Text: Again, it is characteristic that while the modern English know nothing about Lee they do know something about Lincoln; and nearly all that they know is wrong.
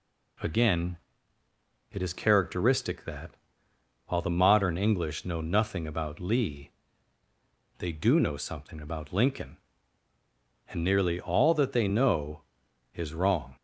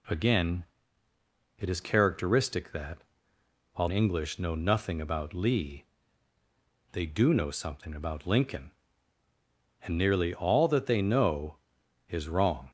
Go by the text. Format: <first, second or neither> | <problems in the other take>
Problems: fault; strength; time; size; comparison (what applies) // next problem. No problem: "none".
first | pauses between "that" and "while"; noticeable; at 2.9 s; 0.76 s long; noticeable in the first // skips "the modern"; at 3.8 s // pauses between "Lee" and "they"; at 5.8 s; 1.0 s long; also in the first